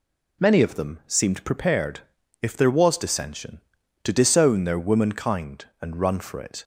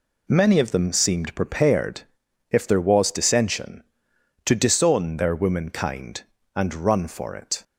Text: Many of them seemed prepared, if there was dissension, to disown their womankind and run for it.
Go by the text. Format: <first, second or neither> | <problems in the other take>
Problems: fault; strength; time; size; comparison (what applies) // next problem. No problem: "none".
neither | none